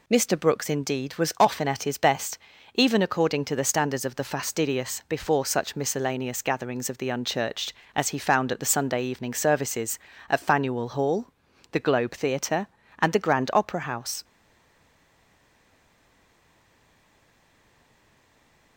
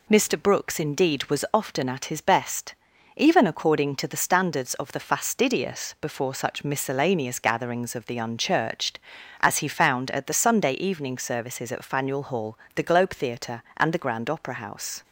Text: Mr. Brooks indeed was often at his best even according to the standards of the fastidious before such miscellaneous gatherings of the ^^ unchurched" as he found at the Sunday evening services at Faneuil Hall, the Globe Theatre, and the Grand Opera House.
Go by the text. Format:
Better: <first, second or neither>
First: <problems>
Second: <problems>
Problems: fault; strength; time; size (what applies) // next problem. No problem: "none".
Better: second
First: pauses between "best" and "even"; at 2.3 s; 0.40 s long // stays silent after the last word; strong; from 14.2 s on; 4.5 s long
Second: pauses between "best" and "even"; at 2.7 s; 0.44 s long